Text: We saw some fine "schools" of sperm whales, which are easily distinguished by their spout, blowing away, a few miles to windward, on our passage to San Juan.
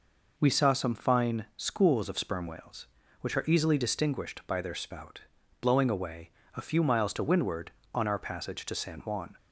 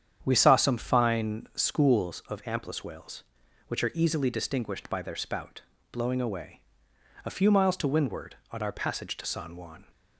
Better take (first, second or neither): first